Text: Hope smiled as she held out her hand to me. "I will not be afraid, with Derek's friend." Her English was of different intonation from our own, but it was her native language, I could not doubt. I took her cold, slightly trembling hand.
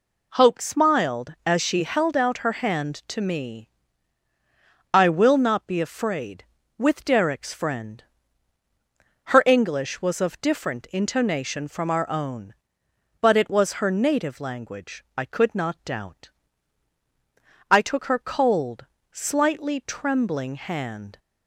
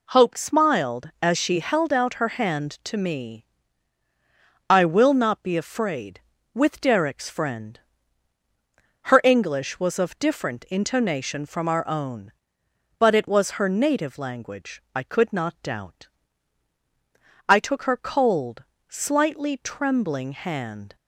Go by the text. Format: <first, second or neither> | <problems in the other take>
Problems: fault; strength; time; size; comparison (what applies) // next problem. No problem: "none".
neither | none